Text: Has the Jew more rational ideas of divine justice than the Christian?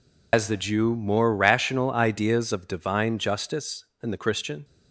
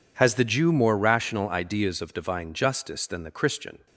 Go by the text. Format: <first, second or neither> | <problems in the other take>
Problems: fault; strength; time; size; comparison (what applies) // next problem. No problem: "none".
second | loses the start of "Has"; at 0.3 s; 90 ms